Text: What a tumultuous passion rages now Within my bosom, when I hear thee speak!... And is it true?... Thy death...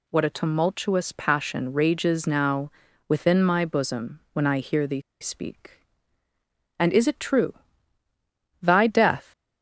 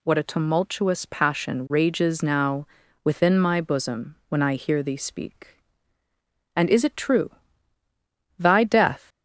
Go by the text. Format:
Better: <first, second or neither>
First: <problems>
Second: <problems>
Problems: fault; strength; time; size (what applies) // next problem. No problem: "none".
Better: second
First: pauses between "now" and "Within"; at 2.7 s; 0.38 s long // pauses between "thee" and "speak"; slight; at 4.9 s; 0.22 s long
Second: pauses between "now" and "Within"; at 2.6 s; 0.38 s long